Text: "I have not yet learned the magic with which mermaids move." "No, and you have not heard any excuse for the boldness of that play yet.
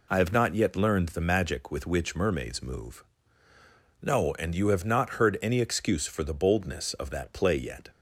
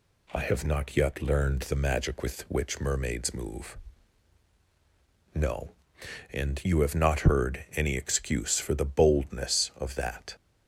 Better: first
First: none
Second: stops before "play yet"; at 10.3 s

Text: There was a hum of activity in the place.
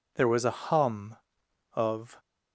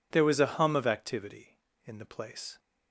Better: second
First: stops before "activity in the place"; at 2.1 s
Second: none

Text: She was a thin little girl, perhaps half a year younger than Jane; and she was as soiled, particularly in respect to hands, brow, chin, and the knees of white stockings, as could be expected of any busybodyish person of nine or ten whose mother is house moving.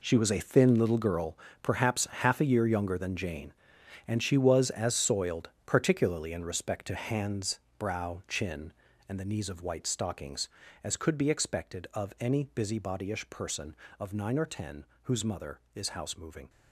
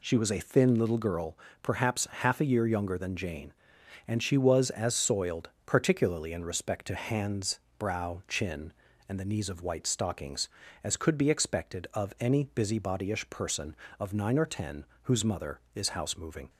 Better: second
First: gets quieter; strong; throughout; 12.5 dB // pauses between "ten" and "whose"; slight; at 14.8 s; 0.18 s long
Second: pauses between "ten" and "whose"; slight; at 14.8 s; 0.18 s long

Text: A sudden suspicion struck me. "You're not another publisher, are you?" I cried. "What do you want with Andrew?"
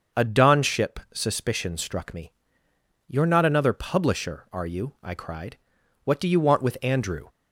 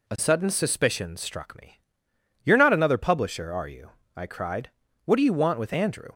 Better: second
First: starts louder than the rest; until 1.2 s; 6.5 dB // says "donship" for "sudden"; at 0.2 s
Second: none

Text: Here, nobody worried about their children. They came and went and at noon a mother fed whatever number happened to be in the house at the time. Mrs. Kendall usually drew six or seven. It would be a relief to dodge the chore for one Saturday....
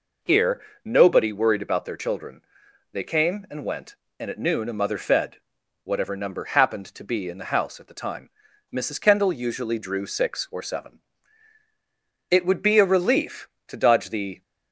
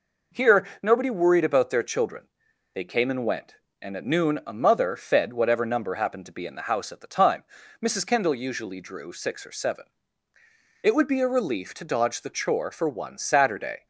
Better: second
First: pauses between "fed" and "whatever"; noticeable; at 5.3 s; 0.46 s long // stops before "chore for one Saturday"; at 14.4 s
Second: none

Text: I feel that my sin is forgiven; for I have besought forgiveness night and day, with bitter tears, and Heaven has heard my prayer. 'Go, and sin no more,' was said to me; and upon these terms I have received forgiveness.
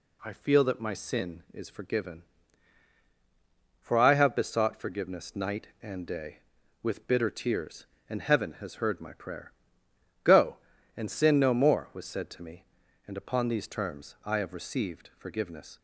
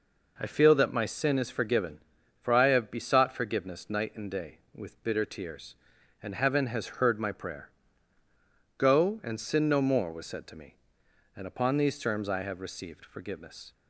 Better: neither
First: none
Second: none

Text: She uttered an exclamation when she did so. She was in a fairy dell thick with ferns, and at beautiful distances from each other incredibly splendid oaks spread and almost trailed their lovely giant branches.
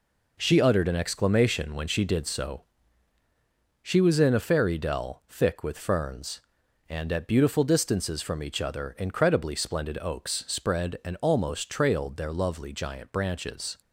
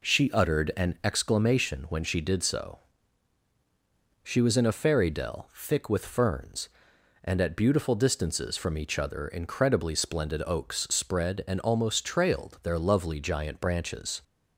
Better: neither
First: none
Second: none

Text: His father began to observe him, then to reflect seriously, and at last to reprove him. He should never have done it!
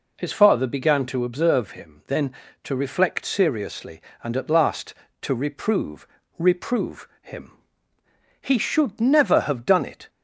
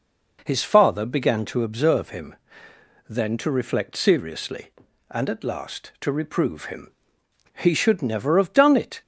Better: second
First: says "reprove" twice; at 6.3 s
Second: none

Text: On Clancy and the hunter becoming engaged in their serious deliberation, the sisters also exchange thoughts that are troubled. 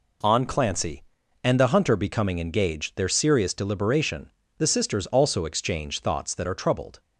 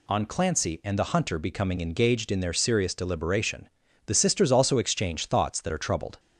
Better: second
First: skips "in"; at 2.9 s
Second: none

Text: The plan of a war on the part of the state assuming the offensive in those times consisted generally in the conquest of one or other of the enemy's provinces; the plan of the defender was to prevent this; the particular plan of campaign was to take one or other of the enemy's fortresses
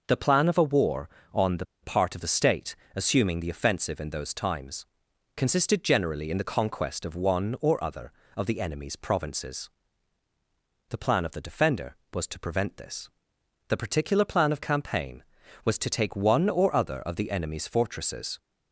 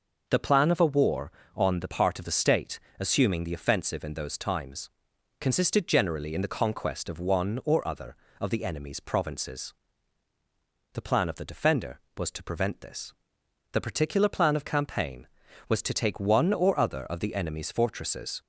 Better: second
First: pauses between "the" and "part"; slight; at 1.6 s; 0.18 s long // pauses between "state" and "assuming"; slight; at 2.7 s; 0.18 s long // pauses between "times" and "consisted"; noticeable; at 4.8 s; 0.50 s long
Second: pauses between "state" and "assuming"; slight; at 2.7 s; 0.18 s long // pauses between "times" and "consisted"; noticeable; at 4.8 s; 0.50 s long

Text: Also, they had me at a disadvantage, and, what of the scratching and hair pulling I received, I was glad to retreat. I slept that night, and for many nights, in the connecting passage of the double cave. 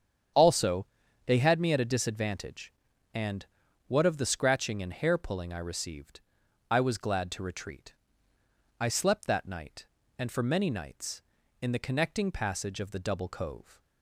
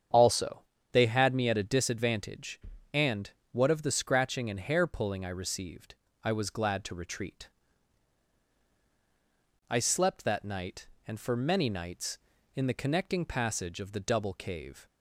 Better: second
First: starts louder than the rest; strong; until 1.7 s; 8.5 dB // says "cove" for "cave"; at 13.2 s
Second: starts louder than the rest; strong; until 1.4 s; 8 dB

